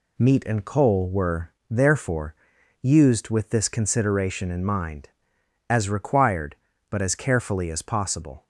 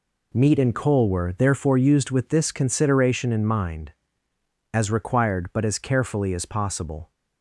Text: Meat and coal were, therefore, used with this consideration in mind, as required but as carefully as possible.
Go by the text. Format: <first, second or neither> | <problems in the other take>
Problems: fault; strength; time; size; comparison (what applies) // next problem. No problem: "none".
neither | none